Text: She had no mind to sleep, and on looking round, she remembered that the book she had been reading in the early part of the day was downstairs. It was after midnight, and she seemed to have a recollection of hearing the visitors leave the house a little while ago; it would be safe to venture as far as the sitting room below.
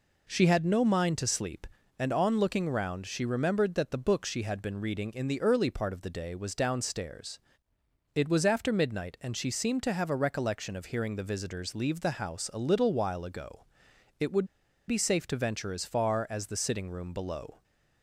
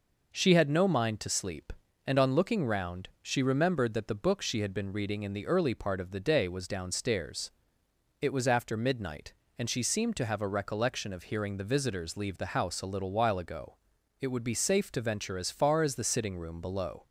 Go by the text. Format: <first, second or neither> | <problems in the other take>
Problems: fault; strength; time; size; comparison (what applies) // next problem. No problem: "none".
second | pauses between "would" and "be"; at 14.4 s; 0.44 s long